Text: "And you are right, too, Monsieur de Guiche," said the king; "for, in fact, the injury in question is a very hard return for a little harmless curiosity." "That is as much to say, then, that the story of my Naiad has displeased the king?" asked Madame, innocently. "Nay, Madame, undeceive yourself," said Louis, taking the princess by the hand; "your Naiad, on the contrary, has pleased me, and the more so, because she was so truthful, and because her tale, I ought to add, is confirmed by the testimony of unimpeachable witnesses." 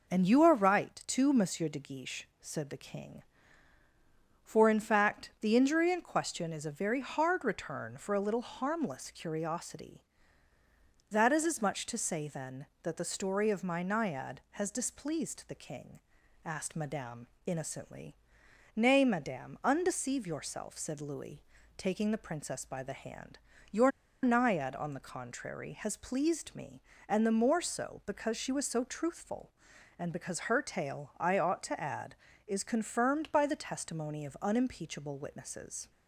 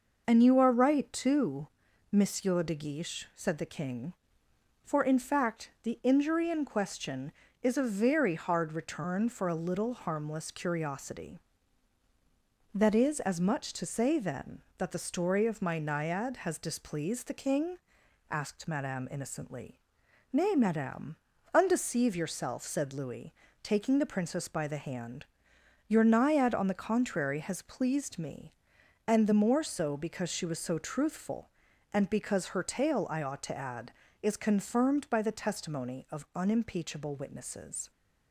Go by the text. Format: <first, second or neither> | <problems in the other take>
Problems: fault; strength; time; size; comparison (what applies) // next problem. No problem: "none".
second | pauses between "your" and "Naiad"; slight; at 23.9 s; 0.33 s long